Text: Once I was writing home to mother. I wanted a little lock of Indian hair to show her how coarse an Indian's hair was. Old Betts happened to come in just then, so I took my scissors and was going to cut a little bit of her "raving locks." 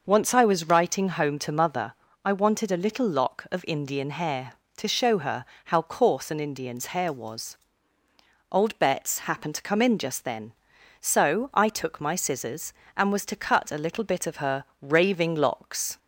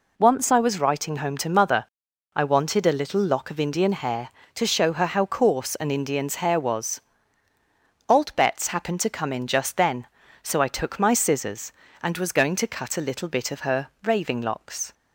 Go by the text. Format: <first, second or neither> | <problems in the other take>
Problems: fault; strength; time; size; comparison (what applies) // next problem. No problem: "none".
second | pauses between "her" and "how"; slight; at 5.4 s; 0.20 s long // skips "going"; at 13.2 s // pauses between "her" and "raving"; slight; at 14.6 s; 0.16 s long